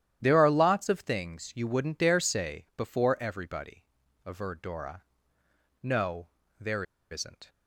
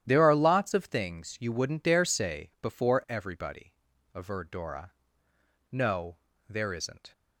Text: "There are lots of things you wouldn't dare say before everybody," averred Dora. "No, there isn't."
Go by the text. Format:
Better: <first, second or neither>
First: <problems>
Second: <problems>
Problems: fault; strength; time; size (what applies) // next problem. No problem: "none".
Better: second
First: starts louder than the rest; strong; until 1.2 s; 11 dB // pauses between "there" and "isn't"; slight; at 6.8 s; 0.27 s long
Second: starts louder than the rest; strong; until 1.0 s; 11 dB